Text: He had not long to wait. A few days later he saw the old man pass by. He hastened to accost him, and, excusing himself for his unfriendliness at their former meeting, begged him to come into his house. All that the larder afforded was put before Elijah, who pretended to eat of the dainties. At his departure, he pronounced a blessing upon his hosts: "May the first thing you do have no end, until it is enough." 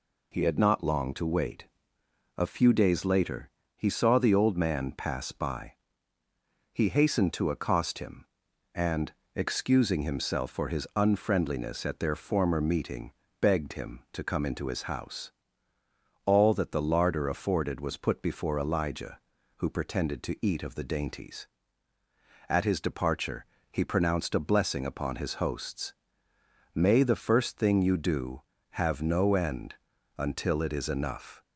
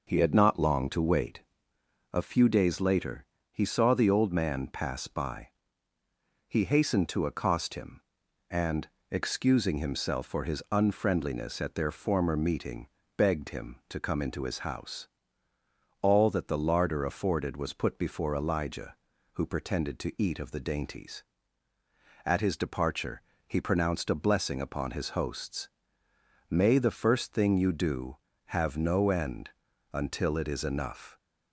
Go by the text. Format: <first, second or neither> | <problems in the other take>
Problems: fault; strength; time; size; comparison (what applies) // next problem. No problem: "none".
first | starts louder than the rest; noticeable; until 1.4 s; 5.5 dB // pauses between "later" and "he"; slight; at 3.2 s; 0.26 s long; slight in the first